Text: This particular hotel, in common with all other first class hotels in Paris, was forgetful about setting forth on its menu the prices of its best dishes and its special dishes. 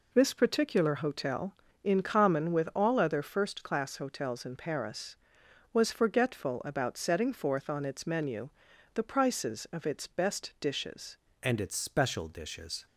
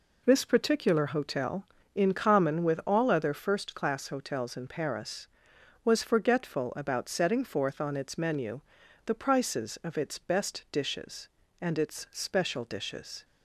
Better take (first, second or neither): second